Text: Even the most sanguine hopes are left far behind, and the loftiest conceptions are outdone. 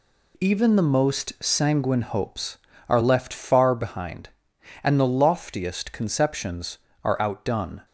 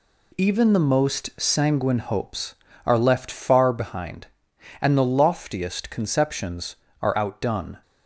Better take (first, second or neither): neither